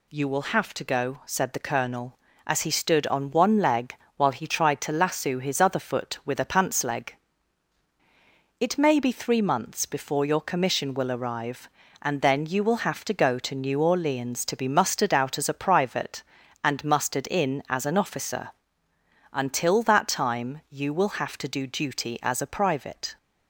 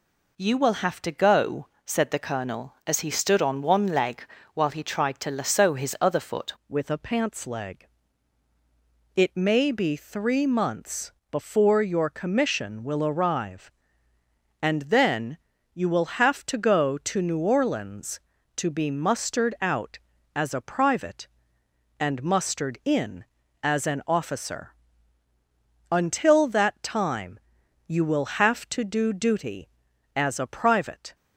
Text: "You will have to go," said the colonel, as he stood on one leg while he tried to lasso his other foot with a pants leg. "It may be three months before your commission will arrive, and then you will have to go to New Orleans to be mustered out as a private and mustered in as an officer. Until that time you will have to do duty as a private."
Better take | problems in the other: first | pauses between "leg" and "while"; slight; at 4.2 s; 0.28 s long; slight in the first // changes voice at "with"; from 6.6 s on; 24.5 s long // pauses between "months" and "before"; slight; at 11.1 s; 0.20 s long // pauses between "then" and "you"; slight; at 15.3 s; 0.36 s long // pauses between "time" and "you"; noticeable; at 27.3 s; 0.48 s long

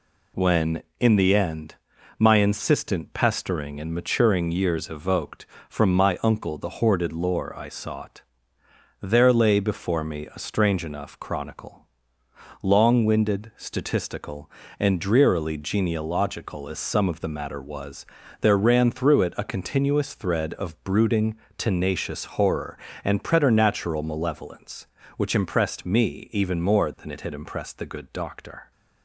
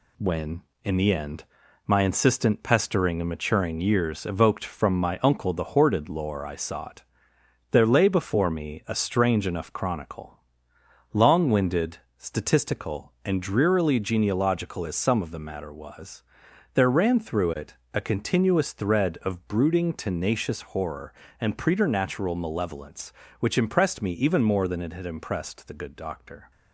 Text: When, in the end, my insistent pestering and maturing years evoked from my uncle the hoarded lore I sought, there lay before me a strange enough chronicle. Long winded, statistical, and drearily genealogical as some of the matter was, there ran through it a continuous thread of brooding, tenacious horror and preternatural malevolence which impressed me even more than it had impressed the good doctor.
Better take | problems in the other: first | gets quieter; noticeable; throughout; 5.5 dB // pauses between "it" and "a"; slight; at 17.7 s; 0.18 s long

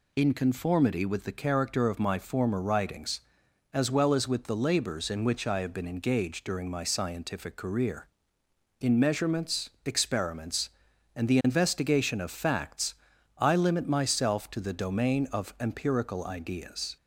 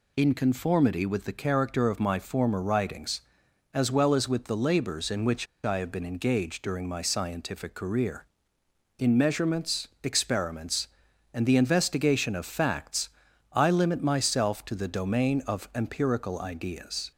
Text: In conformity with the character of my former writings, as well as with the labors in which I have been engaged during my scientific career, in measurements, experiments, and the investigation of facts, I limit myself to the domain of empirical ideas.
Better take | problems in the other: first | pauses between "which" and "I"; slight; at 5.4 s; 0.18 s long

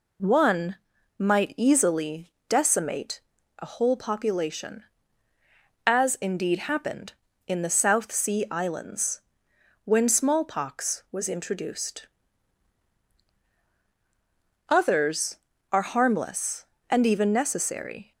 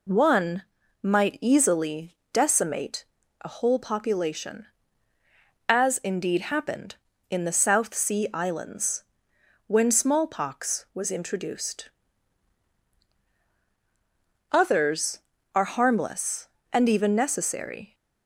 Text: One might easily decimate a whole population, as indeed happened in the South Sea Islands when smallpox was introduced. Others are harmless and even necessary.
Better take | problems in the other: neither | pauses between "One" and "might"; the same in both // pauses between "easily" and "decimate"; slight; the same in both // pauses between "decimate" and "a"; the same in both // pauses between "Islands" and "when"; noticeable; the same in both

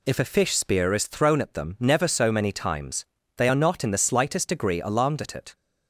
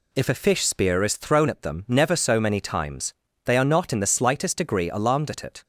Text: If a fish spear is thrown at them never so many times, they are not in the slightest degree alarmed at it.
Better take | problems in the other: neither | none

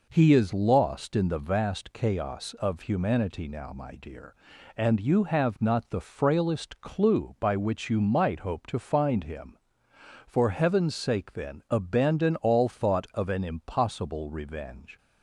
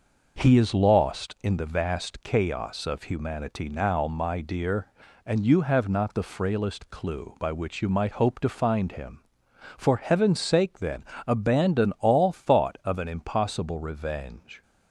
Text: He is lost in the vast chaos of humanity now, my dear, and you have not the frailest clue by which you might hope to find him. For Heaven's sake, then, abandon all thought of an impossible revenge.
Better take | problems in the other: neither | none

